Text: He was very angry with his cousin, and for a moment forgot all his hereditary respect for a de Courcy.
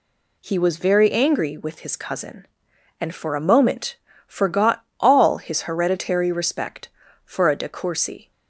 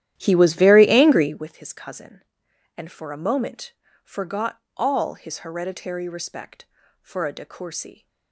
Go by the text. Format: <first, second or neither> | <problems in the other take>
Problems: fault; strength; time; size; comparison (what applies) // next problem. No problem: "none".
first | starts louder than the rest; strong; until 1.5 s; 12 dB // pauses between "moment" and "forgot"; slight; at 3.7 s; 0.30 s long; slight in the first // pauses between "forgot" and "all"; slight; at 4.6 s; 0.16 s long; slight in the first